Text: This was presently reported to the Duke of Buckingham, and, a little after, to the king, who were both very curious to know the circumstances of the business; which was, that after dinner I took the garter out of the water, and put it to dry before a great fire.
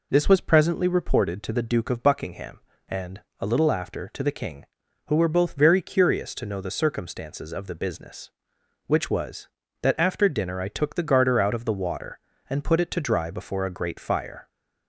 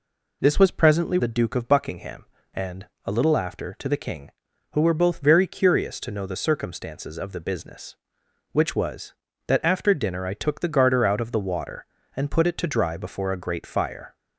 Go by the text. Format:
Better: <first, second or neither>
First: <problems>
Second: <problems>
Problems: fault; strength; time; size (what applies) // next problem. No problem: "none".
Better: first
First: none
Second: skips "reported to"; at 1.1 s